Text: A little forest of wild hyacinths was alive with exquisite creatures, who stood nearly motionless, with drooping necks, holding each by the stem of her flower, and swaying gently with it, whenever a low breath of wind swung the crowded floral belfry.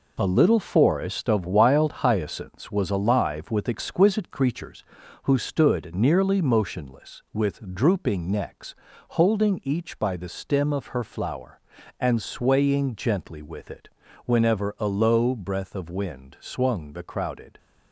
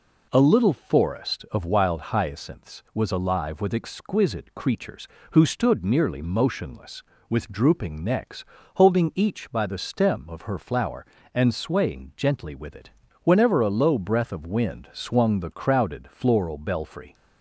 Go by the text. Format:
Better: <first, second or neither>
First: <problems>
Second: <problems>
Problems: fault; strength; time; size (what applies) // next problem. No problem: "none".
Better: second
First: stops before "floral belfry"; at 17.5 s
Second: none